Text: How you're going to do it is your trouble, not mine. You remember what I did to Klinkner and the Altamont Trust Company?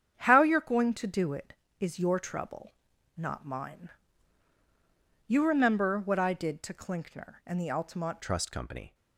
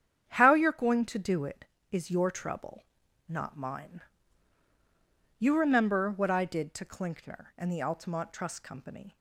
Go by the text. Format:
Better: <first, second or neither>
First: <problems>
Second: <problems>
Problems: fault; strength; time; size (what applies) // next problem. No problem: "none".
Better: second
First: starts louder than the rest; strong; until 1.1 s; 8.5 dB // changes voice at "Trust"; from 8.2 s on; 0.7 s long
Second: starts louder than the rest; strong; until 1.2 s; 9 dB